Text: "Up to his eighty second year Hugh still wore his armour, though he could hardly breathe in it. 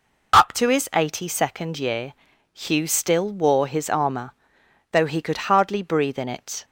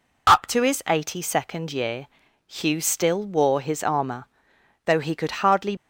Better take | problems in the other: first | pauses between "year" and "Hugh"; at 2.0 s; 0.40 s long; also in the first // stops before "breathe in it"; at 5.7 s

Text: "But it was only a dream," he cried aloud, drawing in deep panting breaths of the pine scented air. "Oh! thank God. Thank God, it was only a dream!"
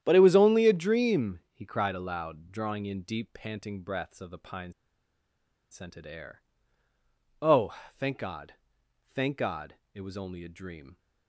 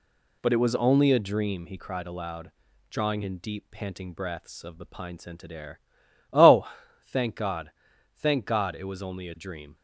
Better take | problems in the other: second | starts louder than the rest; strong; until 1.0 s; 10.5 dB // pauses between "pine" and "scented"; at 4.7 s; 0.99 s long

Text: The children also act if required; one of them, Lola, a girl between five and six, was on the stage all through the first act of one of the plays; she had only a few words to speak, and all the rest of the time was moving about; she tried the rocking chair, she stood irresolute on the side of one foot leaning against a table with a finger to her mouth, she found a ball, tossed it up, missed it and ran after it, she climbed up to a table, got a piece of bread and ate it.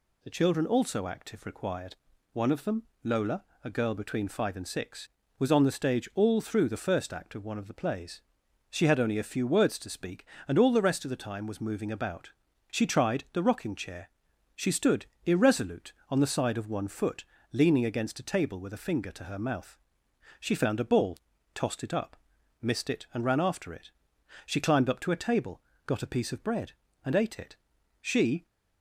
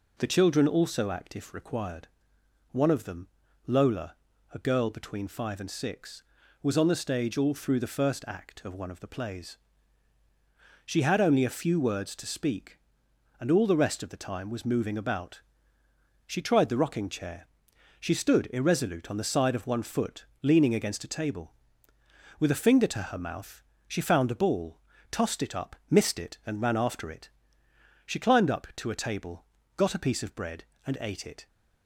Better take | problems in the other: second | pauses between "stood" and "irresolute"; slight; at 15.0 s; 0.18 s long // pauses between "foot" and "leaning"; slight; at 17.2 s; 0.26 s long; slight in the second // goes on to say "She"; slight; from 28.0 s on; 0.42 s long

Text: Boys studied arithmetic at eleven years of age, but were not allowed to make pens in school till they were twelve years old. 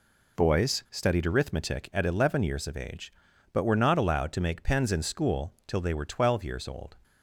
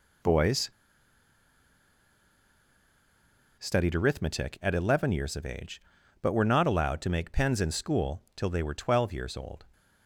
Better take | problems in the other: first | pauses between "Boys" and "studied"; strong; at 0.7 s; 2.8 s long

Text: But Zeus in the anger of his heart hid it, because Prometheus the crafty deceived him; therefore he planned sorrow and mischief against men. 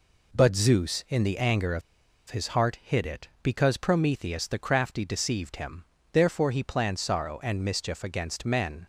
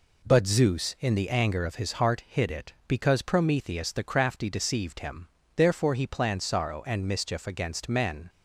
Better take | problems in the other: second | pauses between "of" and "his"; noticeable; at 1.8 s; 0.49 s long

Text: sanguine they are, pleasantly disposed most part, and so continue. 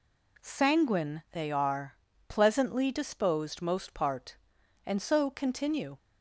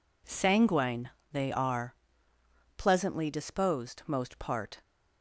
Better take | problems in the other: first | pauses between "sanguine" and "they"; slight; at 1.1 s; 0.22 s long // stops before "and so continue"; at 4.8 s

